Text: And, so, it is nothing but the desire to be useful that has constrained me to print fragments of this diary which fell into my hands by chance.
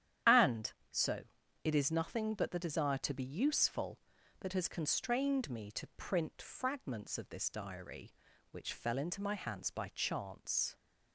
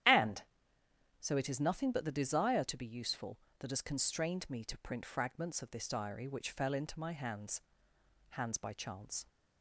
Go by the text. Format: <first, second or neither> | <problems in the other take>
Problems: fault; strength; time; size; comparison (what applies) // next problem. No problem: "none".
first | starts louder than the rest; strong; until 1.8 s; 11 dB; strong in the first // says "hands" twice; at 8.2 s